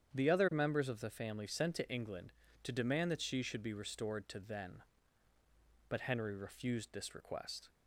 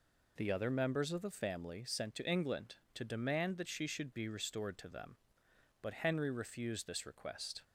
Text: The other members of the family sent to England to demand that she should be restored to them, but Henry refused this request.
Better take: second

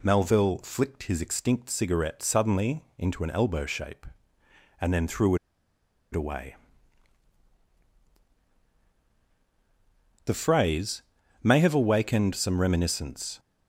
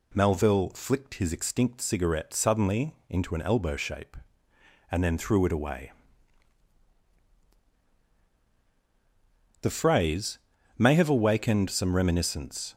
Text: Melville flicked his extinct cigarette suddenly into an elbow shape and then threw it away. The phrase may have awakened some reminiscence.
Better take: second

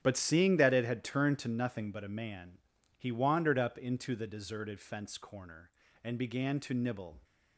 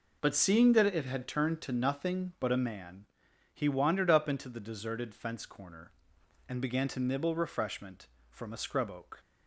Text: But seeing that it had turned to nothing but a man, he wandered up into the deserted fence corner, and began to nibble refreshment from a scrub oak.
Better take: second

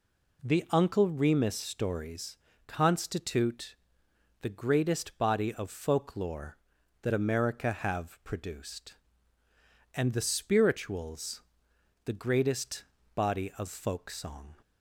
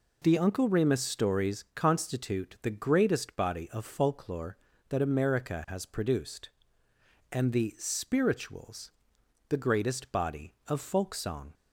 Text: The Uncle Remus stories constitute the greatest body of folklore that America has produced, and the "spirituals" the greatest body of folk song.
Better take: second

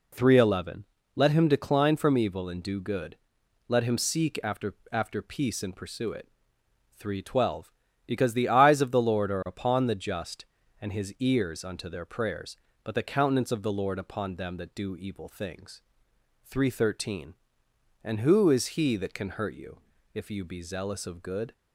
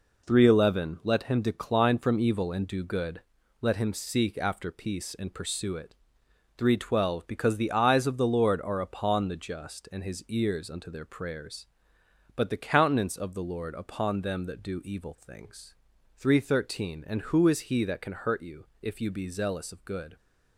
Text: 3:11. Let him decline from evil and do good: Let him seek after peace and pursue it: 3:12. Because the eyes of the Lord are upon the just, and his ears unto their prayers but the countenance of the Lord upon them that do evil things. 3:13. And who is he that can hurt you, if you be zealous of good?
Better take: second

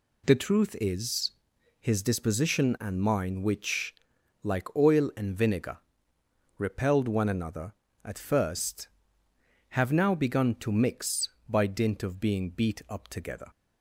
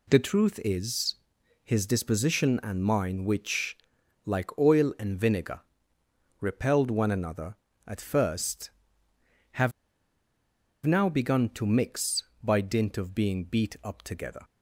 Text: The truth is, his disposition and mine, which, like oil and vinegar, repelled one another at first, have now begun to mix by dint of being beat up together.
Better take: first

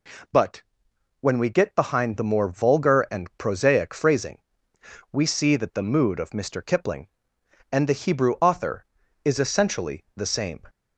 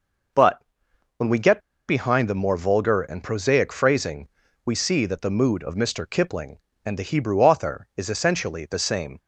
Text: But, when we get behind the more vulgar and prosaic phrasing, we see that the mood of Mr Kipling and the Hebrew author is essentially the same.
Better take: first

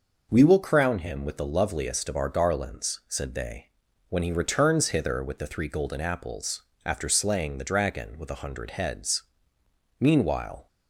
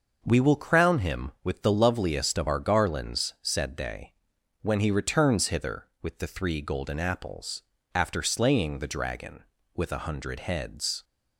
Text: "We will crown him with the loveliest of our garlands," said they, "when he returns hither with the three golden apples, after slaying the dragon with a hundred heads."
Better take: second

